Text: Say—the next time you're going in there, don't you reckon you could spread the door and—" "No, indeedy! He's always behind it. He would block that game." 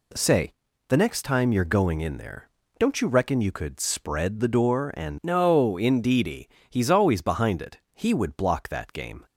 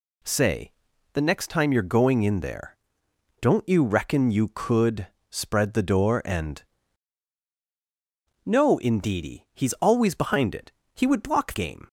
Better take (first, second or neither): first